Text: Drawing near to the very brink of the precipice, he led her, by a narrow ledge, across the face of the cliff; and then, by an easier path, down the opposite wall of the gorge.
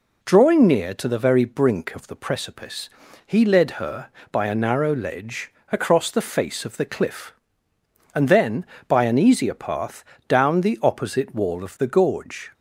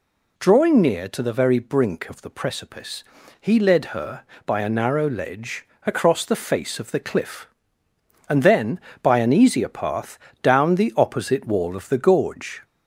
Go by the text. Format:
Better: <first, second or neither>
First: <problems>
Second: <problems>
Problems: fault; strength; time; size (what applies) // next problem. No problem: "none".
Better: first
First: none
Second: gets louder; slight; throughout; 2.5 dB